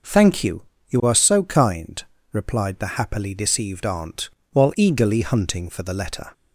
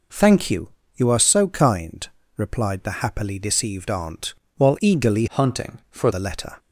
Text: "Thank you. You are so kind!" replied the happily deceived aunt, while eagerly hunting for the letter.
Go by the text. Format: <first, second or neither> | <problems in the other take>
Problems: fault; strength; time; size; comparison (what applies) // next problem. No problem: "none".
first | changes voice from "hunting" to "for"; from 5.2 to 6.0 s; 0.8 s long